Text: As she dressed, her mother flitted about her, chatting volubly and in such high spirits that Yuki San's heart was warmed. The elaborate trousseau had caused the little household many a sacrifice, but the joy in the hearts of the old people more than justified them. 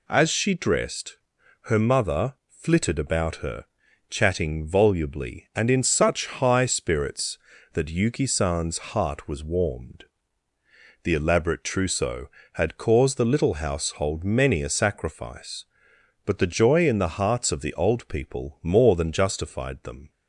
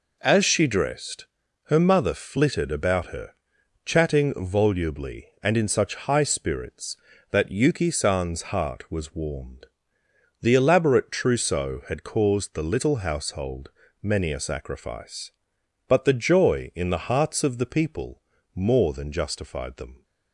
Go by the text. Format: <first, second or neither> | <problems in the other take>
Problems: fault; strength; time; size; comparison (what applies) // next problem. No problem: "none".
first | pauses between "household" and "many"; slight; at 13.7 s; 0.32 s long // skips "old"; at 17.6 s // pauses between "people" and "more"; slight; at 18.2 s; 0.36 s long